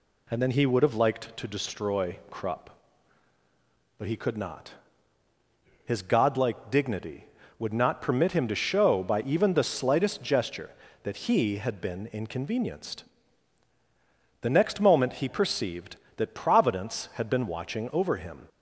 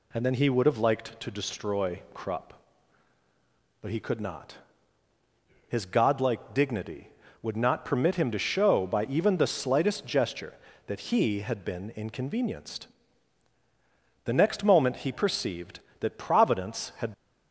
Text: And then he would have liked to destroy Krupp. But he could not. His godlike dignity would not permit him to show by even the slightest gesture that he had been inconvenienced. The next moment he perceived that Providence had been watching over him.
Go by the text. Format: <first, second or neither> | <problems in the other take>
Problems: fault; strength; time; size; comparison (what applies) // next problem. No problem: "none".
first | stops before "been watching over him"; at 17.1 s